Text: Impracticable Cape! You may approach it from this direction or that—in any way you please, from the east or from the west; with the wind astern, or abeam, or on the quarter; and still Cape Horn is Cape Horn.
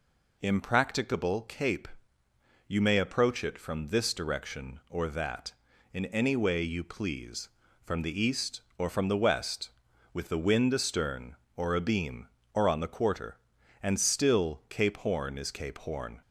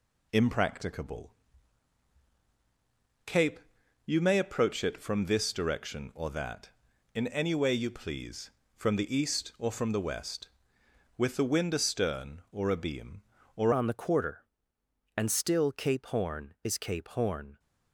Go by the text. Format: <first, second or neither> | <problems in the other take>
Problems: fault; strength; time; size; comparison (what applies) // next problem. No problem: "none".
first | pauses between "Impracticable" and "Cape"; strong; at 1.3 s; 1.9 s long // changes voice at "on"; from 13.7 s on; 3.8 s long